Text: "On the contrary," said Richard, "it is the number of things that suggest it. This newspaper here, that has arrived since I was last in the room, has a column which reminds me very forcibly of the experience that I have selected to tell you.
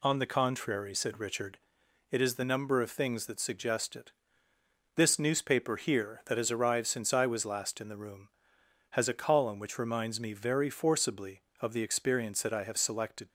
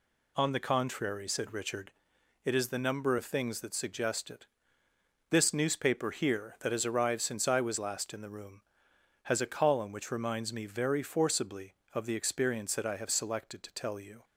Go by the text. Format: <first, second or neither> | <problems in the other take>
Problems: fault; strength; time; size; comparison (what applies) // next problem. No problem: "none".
second | stops before "to tell you"; at 13.2 s